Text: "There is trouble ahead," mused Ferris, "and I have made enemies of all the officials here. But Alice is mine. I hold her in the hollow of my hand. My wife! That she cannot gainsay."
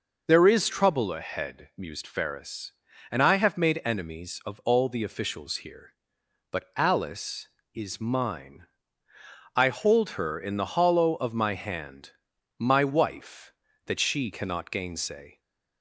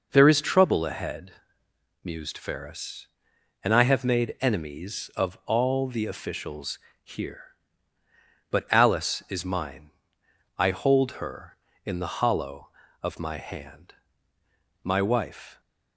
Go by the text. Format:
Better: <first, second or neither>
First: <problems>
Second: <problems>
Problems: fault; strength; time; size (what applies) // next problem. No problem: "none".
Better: first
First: none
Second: pauses between "officials" and "here"; slight; at 6.7 s; 0.24 s long // stops before "That she cannot gainsay"; at 15.5 s